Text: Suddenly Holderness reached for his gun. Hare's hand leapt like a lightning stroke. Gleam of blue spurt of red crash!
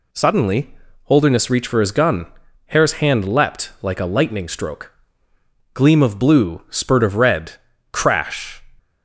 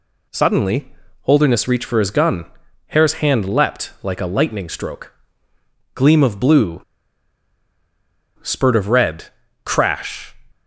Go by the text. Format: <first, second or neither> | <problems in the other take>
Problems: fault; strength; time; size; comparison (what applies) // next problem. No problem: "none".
first | pauses between "Suddenly" and "Holderness"; slight; at 0.9 s; 0.32 s long; slight in the first // pauses between "blue" and "spurt"; strong; at 6.8 s; 1.5 s long // pauses between "red" and "crash"; at 9.2 s; 0.38 s long; also in the first